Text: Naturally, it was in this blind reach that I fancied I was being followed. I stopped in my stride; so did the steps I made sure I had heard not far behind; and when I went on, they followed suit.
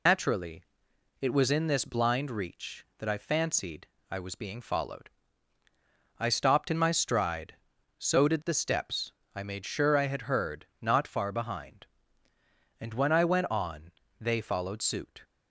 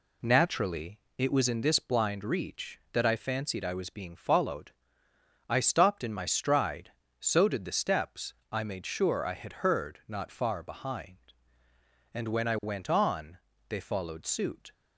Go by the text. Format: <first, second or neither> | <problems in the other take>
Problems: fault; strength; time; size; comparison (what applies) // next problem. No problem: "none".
second | loses the start of "Naturally"; at 0.0 s; 105 ms // pauses between "fancied" and "I"; slight; at 3.8 s; 0.22 s long // pauses between "steps" and "I"; slight; at 9.1 s; 0.24 s long; slight in the second